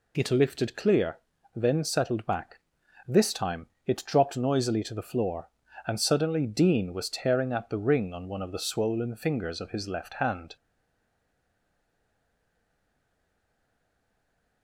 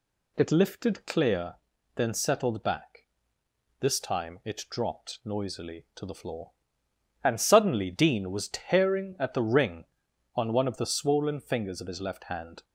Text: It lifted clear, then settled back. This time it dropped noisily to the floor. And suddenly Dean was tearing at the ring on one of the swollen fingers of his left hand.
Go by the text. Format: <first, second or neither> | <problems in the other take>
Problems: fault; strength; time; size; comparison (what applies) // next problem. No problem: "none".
second | pauses between "time" and "it"; slight; at 3.6 s; 0.18 s long // stays silent after the last word; strong; from 10.5 s on; 4.1 s long